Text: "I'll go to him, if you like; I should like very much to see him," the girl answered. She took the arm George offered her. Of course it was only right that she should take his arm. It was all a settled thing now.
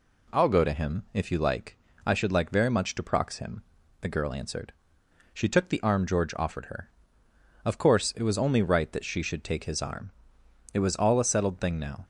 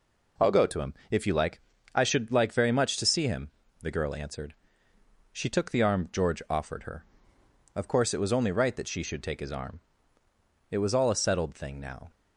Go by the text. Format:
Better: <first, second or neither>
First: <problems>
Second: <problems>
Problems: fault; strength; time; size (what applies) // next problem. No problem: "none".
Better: second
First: says "prox" for "see"; at 3.0 s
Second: none